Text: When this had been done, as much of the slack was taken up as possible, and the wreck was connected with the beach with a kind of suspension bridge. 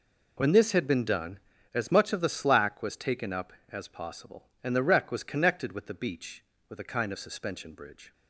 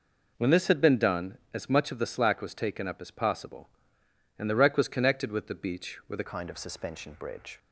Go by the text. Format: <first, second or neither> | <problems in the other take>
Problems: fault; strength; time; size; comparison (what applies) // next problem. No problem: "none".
first | changes voice at "kind"; from 6.2 s on; 1.3 s long